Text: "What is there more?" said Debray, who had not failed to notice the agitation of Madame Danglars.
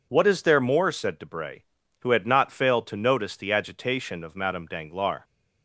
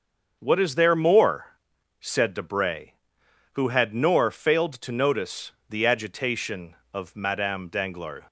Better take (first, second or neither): first